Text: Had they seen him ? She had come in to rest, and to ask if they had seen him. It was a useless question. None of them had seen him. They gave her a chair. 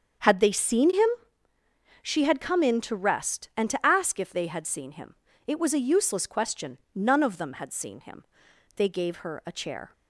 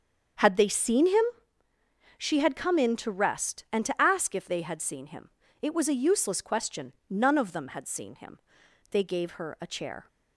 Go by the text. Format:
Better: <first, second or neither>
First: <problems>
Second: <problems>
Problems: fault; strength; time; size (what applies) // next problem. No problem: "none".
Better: neither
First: starts louder than the rest; until 2.2 s; 7 dB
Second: starts louder than the rest; until 2.3 s; 7 dB